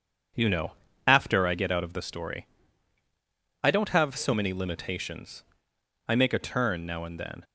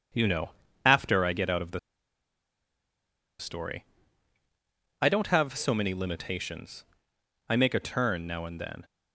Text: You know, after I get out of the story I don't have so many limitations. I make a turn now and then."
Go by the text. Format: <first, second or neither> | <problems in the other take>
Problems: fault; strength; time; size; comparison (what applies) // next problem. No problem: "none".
first | pauses between "the" and "story"; strong; at 1.7 s; 1.6 s long // pauses between "story" and "I"; at 3.8 s; 1.1 s long; also in the first